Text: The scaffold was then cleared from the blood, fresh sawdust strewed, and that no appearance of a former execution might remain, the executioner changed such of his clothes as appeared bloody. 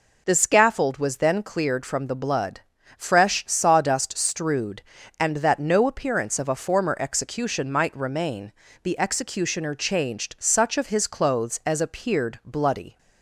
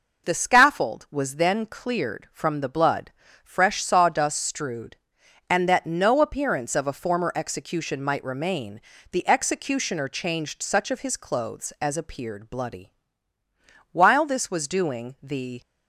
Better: first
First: none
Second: goes on to say "While this was doing the"; strong; from 13.9 s on; 1.6 s long

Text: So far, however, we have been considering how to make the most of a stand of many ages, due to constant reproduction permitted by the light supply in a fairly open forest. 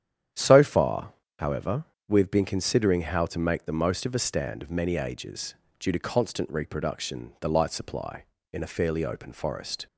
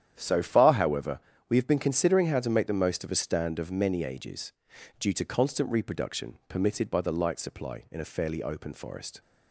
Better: second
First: starts louder than the rest; strong; until 1.6 s; 9.5 dB // skips "permitted by"; at 7.3 s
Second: starts louder than the rest; strong; until 1.1 s; 10 dB

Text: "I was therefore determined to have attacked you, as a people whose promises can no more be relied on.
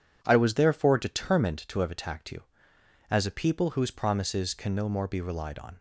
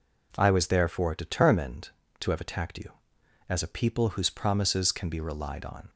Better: first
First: none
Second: skips "no more"; at 5.0 s

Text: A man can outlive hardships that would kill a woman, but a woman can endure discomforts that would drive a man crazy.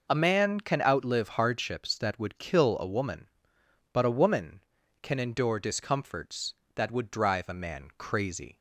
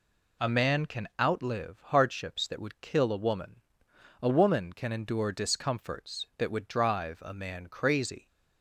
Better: first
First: none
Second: skips "but"; at 3.9 s

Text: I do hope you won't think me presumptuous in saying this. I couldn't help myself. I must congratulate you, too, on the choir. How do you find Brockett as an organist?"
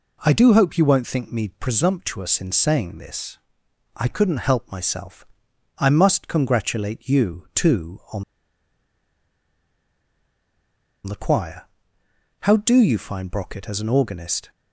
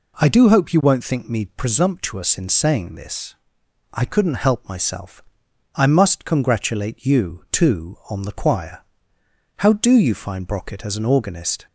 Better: second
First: pauses between "on" and "the"; strong; at 8.2 s; 2.8 s long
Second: none

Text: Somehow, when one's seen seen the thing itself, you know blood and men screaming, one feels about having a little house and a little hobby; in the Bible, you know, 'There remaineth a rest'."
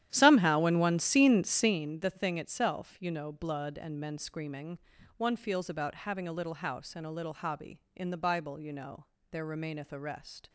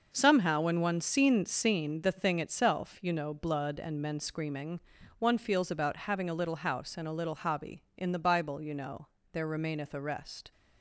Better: second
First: starts louder than the rest; strong; until 1.9 s; 11.5 dB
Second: none

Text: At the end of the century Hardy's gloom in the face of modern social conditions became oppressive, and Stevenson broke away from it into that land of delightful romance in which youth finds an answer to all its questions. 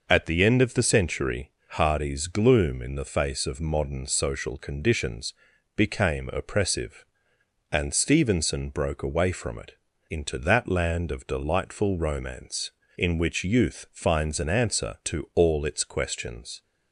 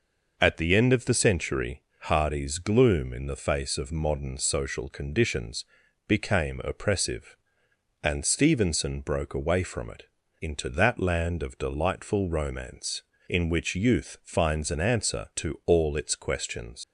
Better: first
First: pauses between "century" and "Hardy's"; slight; at 1.4 s; 0.20 s long // pauses between "conditions" and "became"; at 5.3 s; 0.44 s long // pauses between "it" and "into"; at 9.7 s; 0.38 s long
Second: pauses between "century" and "Hardy's"; slight; at 1.8 s; 0.20 s long // pauses between "conditions" and "became"; at 5.6 s; 0.44 s long // pauses between "it" and "into"; at 10.0 s; 0.38 s long // leaves "questions" unfinished; at 16.8 s; 95 ms

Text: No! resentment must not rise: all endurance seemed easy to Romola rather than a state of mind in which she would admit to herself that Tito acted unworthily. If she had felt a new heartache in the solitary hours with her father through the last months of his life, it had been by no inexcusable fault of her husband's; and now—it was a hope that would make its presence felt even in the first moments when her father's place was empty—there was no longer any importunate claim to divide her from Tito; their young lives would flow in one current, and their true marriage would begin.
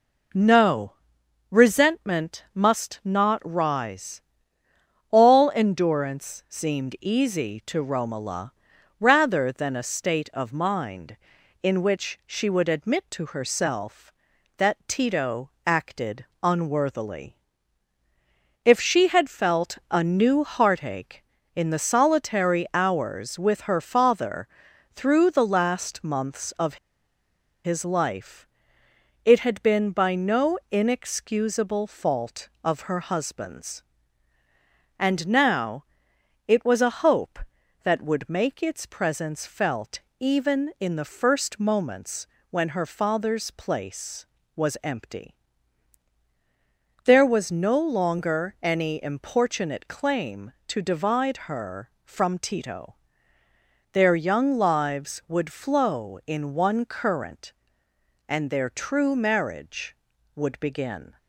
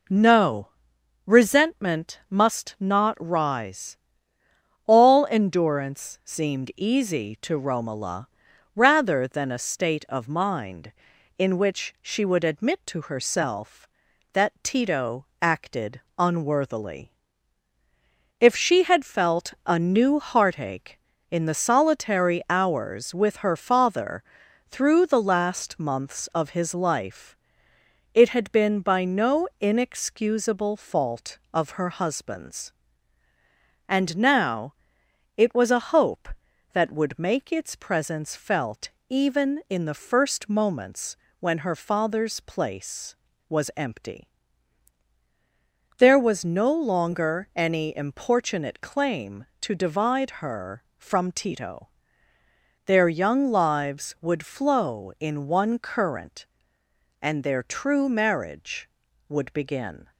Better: second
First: pauses between "Romola" and "rather"; at 8.5 s; 0.44 s long // pauses between "Tito" and "acted"; slight; at 15.4 s; 0.16 s long // pauses between "acted" and "unworthily"; slight; at 16.2 s; 0.18 s long // pauses between "father" and "through"; noticeable; at 24.4 s; 0.48 s long // pauses between "of" and "his"; noticeable; at 26.7 s; 0.88 s long // pauses between "felt" and "even"; slight; at 39.9 s; 0.18 s long // pauses between "moments" and "when"; slight; at 42.2 s; 0.26 s long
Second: pauses between "Romola" and "rather"; at 8.2 s; 0.44 s long // pauses between "Tito" and "acted"; slight; at 15.2 s; 0.16 s long // pauses between "acted" and "unworthily"; slight; at 15.9 s; 0.18 s long // pauses between "father" and "through"; noticeable; at 24.2 s; 0.48 s long // pauses between "felt" and "even"; slight; at 38.8 s; 0.18 s long // pauses between "moments" and "when"; slight; at 41.1 s; 0.26 s long

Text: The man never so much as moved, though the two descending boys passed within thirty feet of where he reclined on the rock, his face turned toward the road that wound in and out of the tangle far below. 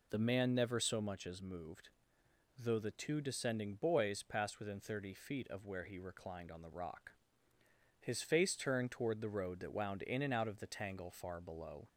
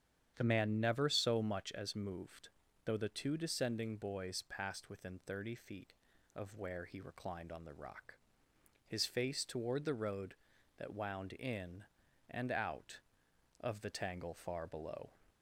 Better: first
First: none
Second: starts louder than the rest; strong; until 1.3 s; 9 dB // skips "turned"; at 9.4 s

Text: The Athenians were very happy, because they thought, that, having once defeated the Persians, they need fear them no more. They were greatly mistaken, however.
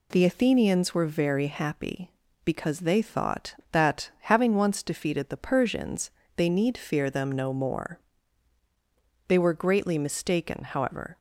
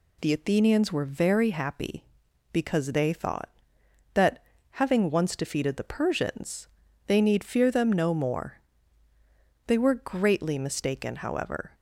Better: neither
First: none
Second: none

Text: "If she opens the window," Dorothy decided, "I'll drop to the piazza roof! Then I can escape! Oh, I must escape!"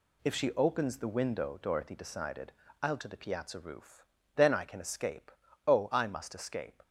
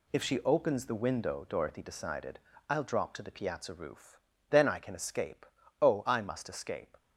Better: second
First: skips "drop"; at 2.9 s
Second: none

